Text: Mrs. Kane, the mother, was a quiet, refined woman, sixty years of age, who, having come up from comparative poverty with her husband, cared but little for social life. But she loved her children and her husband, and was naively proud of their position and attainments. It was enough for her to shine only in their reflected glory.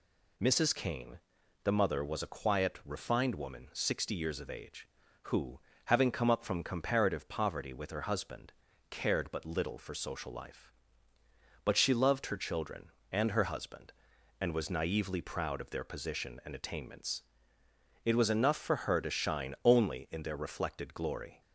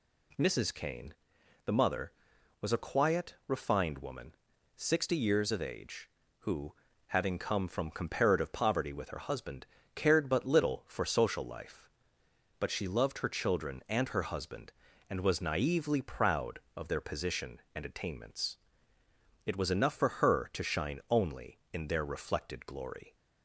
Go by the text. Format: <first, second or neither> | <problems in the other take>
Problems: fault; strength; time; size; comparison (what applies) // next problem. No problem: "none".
first | skips "up"; at 7.6 s